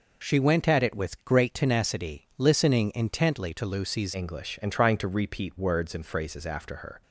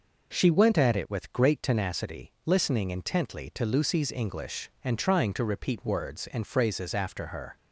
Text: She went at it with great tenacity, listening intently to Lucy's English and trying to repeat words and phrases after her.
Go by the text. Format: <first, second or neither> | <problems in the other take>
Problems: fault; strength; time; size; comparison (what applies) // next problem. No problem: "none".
second | changes voice at "English"; from 4.1 s on; 2.9 s long